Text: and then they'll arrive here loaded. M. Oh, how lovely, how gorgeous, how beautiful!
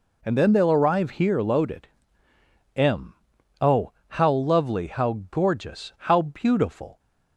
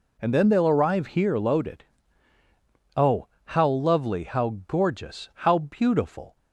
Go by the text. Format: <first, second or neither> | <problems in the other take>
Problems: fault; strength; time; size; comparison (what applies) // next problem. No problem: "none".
first | skips "M"; at 2.3 s